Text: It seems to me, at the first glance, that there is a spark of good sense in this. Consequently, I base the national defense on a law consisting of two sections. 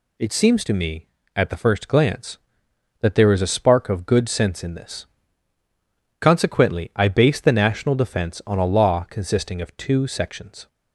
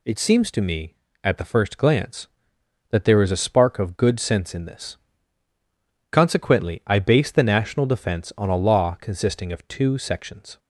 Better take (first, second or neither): neither